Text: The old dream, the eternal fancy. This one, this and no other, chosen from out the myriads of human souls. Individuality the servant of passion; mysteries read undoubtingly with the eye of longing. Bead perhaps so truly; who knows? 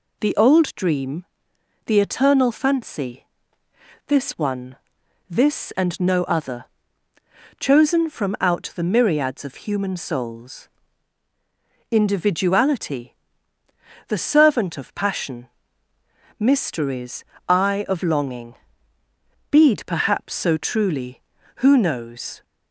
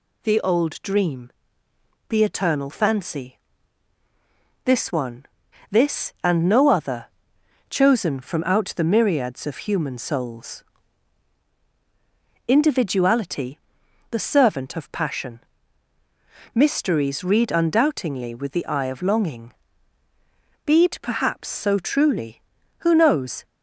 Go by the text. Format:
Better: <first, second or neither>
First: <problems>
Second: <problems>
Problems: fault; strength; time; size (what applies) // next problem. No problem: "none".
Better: second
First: pauses between "Individuality" and "the"; noticeable; at 13.1 s; 0.94 s long // skips "read undoubtingly with the"; at 17.3 s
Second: pauses between "Individuality" and "the"; noticeable; at 13.5 s; 0.54 s long